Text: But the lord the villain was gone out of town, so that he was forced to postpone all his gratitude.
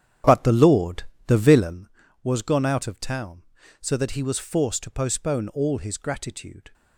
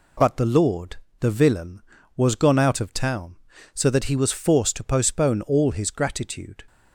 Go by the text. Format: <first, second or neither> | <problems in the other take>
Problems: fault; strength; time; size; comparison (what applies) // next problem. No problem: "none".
second | starts louder than the rest; strong; until 1.9 s; 10 dB // pauses between "lord" and "the"; slight; at 1.0 s; 0.24 s long; slight in the second